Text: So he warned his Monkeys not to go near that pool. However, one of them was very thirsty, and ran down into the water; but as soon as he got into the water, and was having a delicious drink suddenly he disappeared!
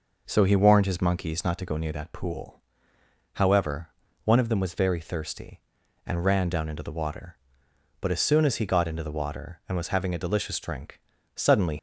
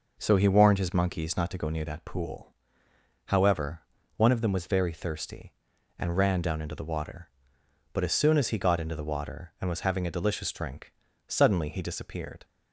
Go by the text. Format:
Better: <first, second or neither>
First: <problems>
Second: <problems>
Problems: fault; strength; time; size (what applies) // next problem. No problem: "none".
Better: second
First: pauses between "drink" and "suddenly"; at 10.9 s; 0.38 s long // stops before "he disappeared"; at 11.7 s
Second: pauses between "drink" and "suddenly"; at 10.9 s; 0.38 s long